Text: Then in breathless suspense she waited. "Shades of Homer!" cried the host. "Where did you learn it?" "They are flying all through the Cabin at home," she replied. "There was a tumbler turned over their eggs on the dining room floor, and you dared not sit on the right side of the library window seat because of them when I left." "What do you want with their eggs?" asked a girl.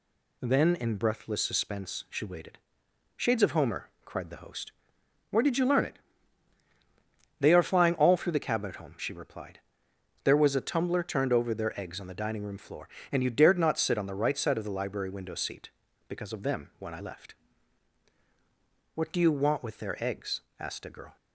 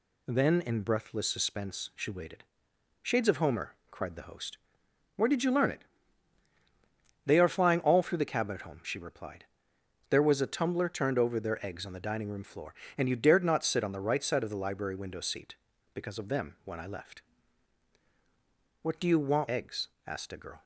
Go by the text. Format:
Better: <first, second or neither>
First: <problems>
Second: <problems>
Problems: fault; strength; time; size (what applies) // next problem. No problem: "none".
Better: first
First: none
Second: skips "with their"; at 19.4 s